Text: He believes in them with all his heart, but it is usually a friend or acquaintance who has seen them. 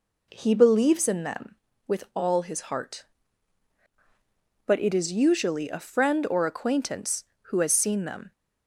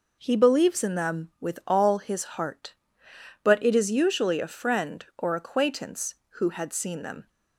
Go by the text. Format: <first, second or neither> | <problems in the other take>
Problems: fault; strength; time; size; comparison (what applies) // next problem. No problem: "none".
first | says "had" for "has"; at 6.4 s